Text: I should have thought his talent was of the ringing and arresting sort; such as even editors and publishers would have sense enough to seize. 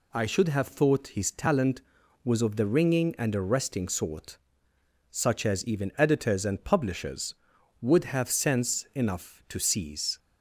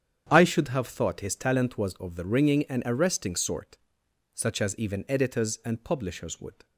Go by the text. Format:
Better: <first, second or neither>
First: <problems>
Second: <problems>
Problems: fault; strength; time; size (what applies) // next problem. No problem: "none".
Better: first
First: none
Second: starts louder than the rest; strong; until 1.3 s; 8.5 dB // stops before "have sense enough to seize"; at 6.6 s